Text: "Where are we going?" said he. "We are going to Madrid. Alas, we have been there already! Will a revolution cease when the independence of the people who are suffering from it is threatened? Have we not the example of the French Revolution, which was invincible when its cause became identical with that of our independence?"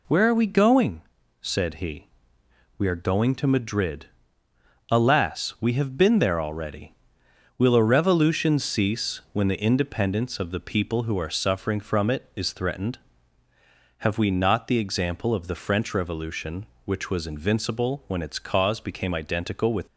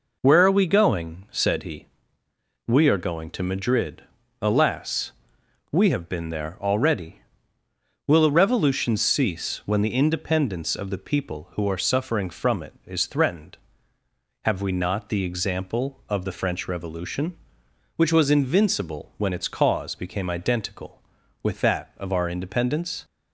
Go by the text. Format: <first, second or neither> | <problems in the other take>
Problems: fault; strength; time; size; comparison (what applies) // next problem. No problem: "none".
second | stops before "that of our independence"; at 19.8 s